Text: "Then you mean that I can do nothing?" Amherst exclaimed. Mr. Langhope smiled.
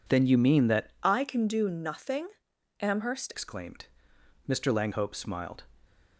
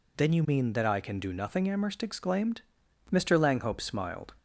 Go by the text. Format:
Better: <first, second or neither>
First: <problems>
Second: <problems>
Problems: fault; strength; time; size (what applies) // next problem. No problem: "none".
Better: second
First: changes voice from "I" to "Amherst"; from 1.0 to 3.3 s; 2.3 s long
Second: none